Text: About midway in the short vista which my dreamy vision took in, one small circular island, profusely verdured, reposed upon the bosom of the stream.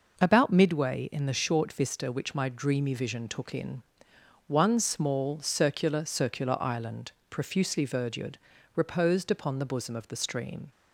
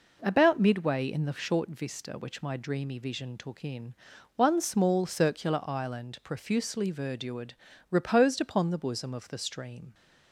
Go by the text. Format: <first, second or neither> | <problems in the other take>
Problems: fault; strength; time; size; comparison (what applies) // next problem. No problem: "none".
second | says "circular" twice; at 6.0 s